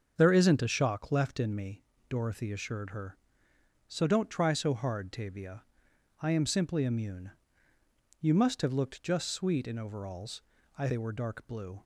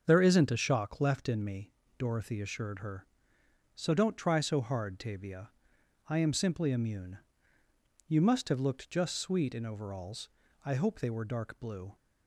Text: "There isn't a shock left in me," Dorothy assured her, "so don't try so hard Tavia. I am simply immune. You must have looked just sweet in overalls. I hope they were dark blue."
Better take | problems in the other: second | starts louder than the rest; until 1.1 s; 6.5 dB; also in the second // skips "hope"; at 10.8 s

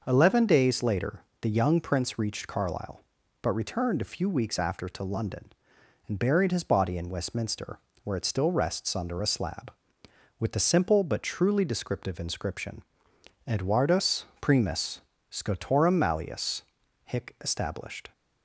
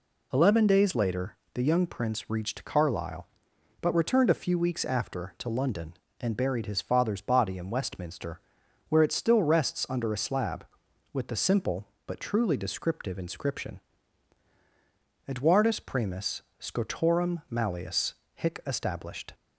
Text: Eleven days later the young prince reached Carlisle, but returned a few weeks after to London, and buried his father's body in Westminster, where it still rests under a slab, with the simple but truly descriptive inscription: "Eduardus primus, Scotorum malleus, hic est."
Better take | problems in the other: second | pauses between "later" and "the"; slight; at 1.2 s; 0.20 s long; slight in the second // skips "father's"; at 6.6 s // pauses between "Eduardus" and "primus"; slight; at 14.2 s; 0.16 s long

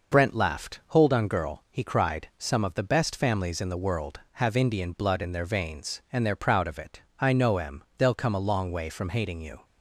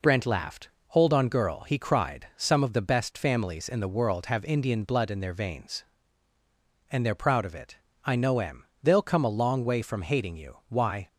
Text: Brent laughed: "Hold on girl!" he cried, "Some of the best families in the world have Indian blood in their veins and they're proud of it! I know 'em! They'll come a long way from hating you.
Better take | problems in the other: first | goes on to say "Why"; slight; from 10.6 s on; 0.40 s long

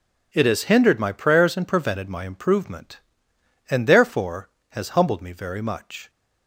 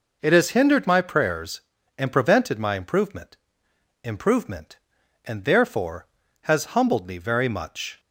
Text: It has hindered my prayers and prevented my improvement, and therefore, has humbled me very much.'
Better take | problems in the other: first | says "improvement" twice; at 4.0 s

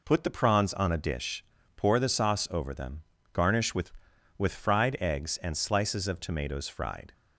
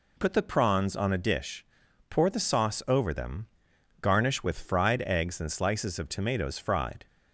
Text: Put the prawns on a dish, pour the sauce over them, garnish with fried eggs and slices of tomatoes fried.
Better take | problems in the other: second | says "with" twice; at 4.3 s

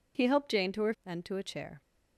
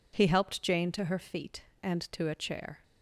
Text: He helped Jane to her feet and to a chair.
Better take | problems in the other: second | skips "feet"; at 0.9 s

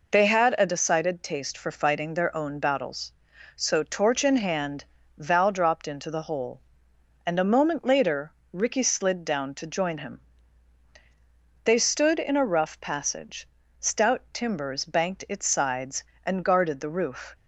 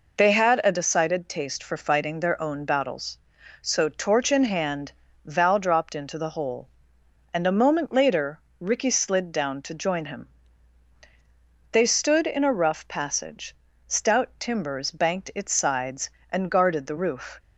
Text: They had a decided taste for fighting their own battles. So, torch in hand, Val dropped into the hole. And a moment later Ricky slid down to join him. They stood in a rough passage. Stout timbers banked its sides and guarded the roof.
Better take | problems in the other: neither | pauses between "later" and "Ricky"; slight; the same in both

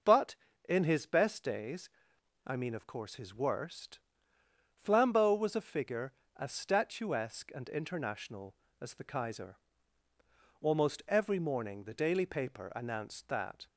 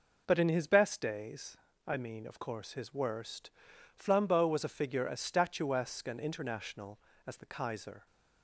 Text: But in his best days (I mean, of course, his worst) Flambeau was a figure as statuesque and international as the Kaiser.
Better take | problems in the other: second | goes on to say "Almost every morning the daily paper announced that"; strong; from 10.6 s on; 3.0 s long

